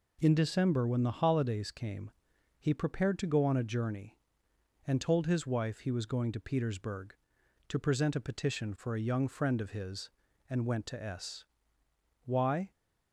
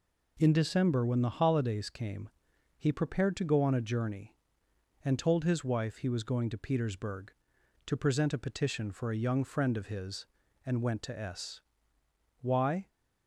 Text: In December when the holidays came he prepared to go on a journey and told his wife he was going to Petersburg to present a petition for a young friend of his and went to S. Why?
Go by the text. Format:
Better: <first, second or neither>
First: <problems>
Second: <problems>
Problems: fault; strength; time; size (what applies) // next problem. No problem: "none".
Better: neither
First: pauses between "came" and "he"; noticeable; at 2.0 s; 0.50 s long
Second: pauses between "came" and "he"; noticeable; at 2.2 s; 0.50 s long